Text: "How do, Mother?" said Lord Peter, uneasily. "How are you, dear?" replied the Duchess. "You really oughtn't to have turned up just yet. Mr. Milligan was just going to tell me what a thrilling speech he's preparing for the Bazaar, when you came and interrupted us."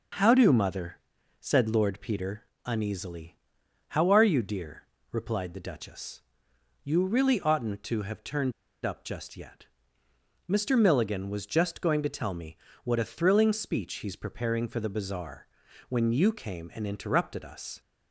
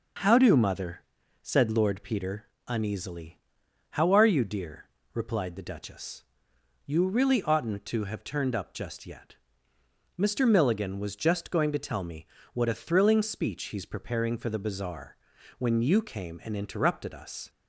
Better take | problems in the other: second | starts louder than the rest; noticeable; until 1.6 s; 6 dB; noticeable in the second // pauses between "turned" and "up"; slight; at 8.5 s; 0.31 s long // pauses between "me" and "what"; slight; at 12.5 s; 0.26 s long; slight in the second

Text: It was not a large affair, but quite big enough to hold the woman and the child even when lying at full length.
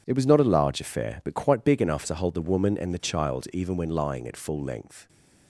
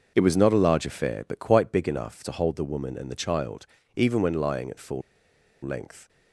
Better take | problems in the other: first | pauses between "child" and "even"; slight; at 3.6 s; 0.30 s long // pauses between "full" and "length"; noticeable; at 5.0 s; 0.62 s long

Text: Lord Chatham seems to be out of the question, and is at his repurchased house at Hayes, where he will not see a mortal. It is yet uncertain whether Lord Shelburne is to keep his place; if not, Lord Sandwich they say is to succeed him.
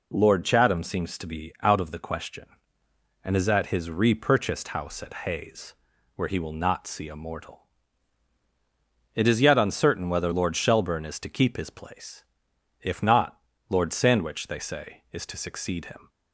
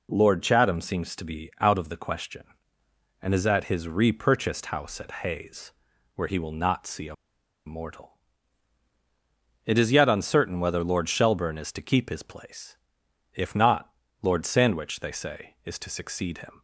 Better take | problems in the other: first | pauses between "a" and "mortal"; noticeable; at 7.1 s; 0.52 s long

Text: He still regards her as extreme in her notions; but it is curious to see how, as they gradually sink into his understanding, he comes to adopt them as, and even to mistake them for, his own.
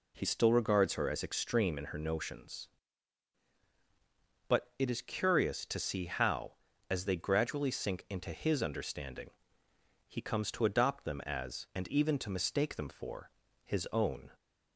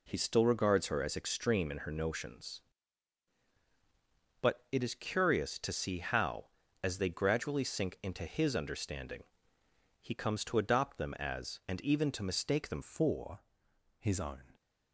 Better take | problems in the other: first | changes voice at "for"; from 12.8 s on; 1.7 s long

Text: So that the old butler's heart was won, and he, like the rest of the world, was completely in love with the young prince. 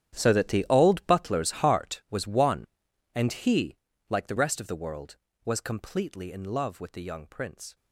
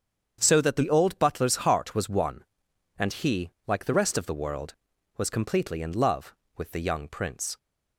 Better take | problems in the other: second | gets quieter; strong; throughout; 17 dB // starts louder than the rest; strong; until 1.2 s; 11 dB; strong in the second

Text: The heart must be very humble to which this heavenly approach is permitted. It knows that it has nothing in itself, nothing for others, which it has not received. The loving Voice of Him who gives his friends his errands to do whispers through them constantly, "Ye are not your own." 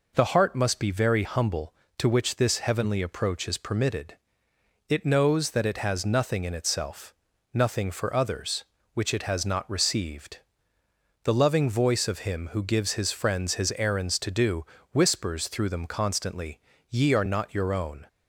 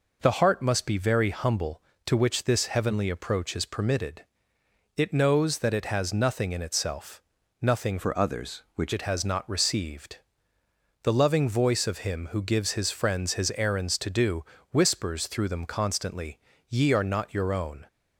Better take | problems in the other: first | changes voice from "for" to "which"; from 7.9 to 8.9 s; 1.0 s long // pauses between "do" and "whispers"; slight; at 14.4 s; 0.26 s long; slight in the first

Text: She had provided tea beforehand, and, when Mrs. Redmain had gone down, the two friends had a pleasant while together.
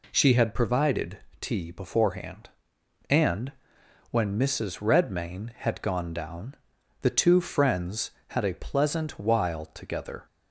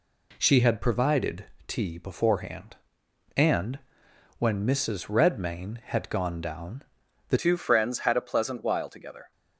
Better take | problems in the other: first | pauses between "provided" and "tea"; slight; at 1.4 s; 0.22 s long; slight in the first // changes voice at "two"; from 7.3 s on; 2.0 s long

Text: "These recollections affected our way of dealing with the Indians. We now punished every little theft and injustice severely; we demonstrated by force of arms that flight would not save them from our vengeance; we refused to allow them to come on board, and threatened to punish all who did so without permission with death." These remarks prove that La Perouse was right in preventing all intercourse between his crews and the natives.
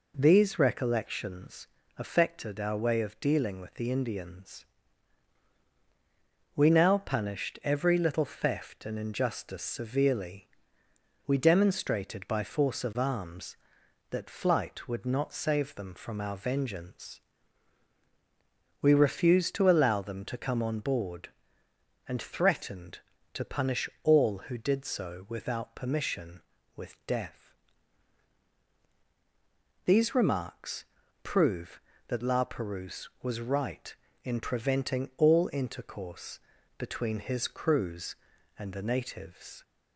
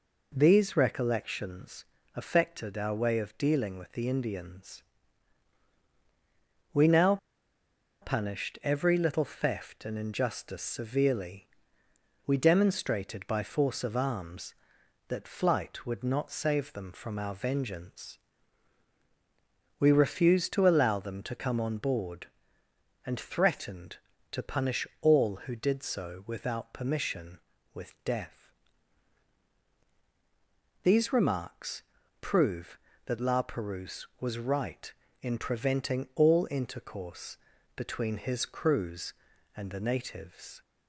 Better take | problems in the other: first | pauses between "recollections" and "affected"; slight; at 1.8 s; 0.30 s long; slight in the first // pauses between "now" and "punished"; noticeable; at 7.1 s; 0.84 s long // pauses between "remarks" and "prove"; at 31.8 s; 0.40 s long; also in the first // pauses between "intercourse" and "between"; slight; at 37.3 s; 0.36 s long; slight in the first

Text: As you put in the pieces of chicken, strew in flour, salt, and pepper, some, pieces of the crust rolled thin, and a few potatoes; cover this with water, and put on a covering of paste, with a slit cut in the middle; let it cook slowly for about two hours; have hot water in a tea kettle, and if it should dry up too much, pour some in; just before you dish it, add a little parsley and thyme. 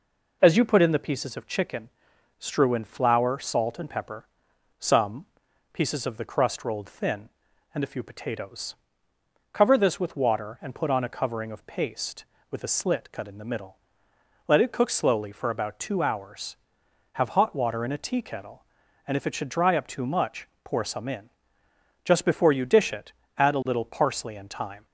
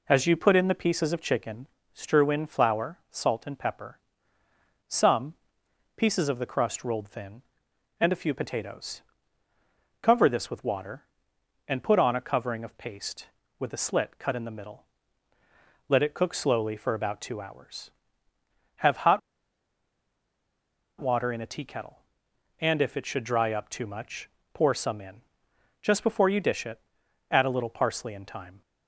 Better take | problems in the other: first | pauses between "hot" and "water"; strong; at 19.1 s; 1.8 s long

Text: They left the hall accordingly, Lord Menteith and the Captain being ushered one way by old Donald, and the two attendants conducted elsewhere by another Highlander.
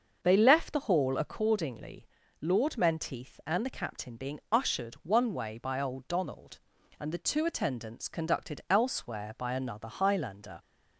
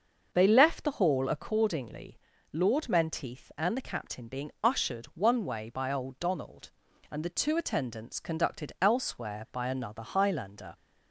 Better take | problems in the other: neither | starts louder than the rest; the same in both

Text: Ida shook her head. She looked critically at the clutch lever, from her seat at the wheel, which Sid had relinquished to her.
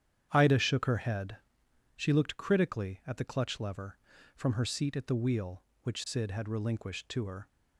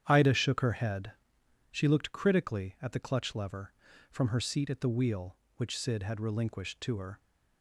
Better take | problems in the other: neither | starts louder than the rest; strong; the same in both

